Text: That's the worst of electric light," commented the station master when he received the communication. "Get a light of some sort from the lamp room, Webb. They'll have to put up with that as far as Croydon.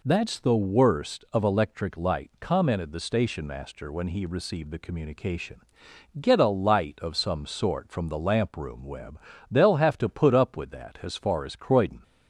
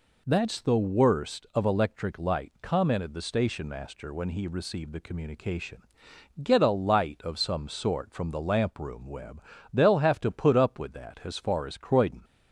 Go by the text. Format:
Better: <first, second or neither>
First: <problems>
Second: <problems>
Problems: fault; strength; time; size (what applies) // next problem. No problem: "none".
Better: neither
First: none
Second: none